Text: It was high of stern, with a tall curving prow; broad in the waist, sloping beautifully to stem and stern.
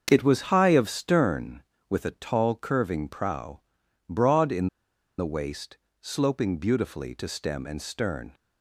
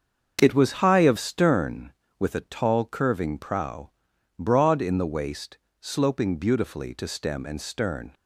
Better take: second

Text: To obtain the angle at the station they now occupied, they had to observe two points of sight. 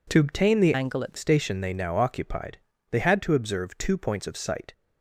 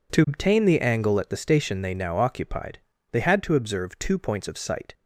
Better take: second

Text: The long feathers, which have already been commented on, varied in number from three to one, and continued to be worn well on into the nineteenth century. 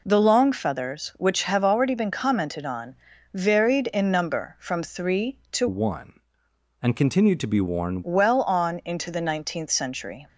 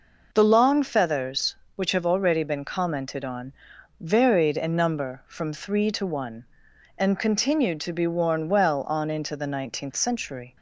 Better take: second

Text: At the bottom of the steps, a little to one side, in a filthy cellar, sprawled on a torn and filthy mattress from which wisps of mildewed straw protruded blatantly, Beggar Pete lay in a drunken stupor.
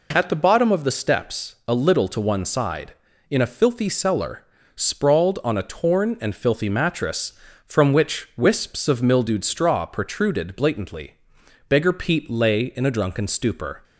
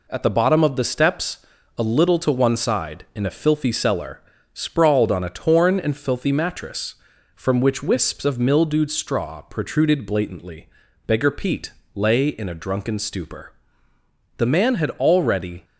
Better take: first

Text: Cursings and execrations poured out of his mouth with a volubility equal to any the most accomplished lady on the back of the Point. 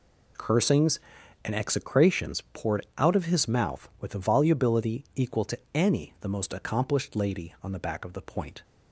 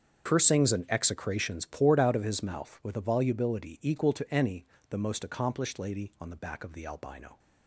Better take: first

